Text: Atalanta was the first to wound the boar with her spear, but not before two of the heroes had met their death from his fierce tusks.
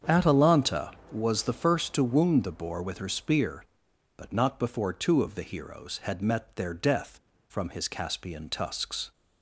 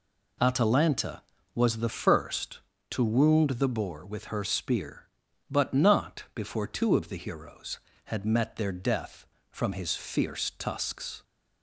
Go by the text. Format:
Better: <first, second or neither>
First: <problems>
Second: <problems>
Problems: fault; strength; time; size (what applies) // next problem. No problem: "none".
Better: second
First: starts louder than the rest; strong; until 1.3 s; 7.5 dB // says "caspian" for "fierce"; at 7.8 s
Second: none